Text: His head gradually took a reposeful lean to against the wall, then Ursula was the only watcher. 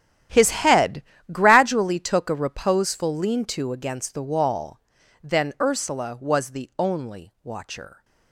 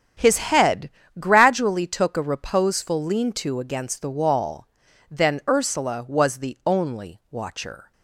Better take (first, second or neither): second